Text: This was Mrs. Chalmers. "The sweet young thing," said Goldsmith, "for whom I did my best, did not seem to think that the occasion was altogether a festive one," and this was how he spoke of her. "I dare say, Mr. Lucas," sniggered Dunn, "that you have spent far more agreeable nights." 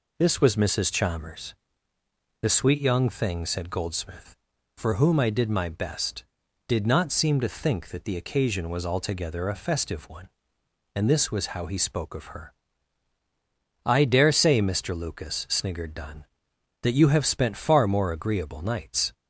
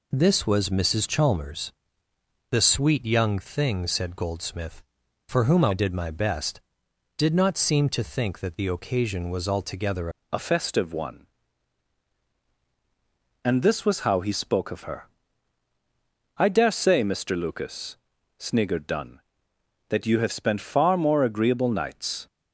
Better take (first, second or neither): first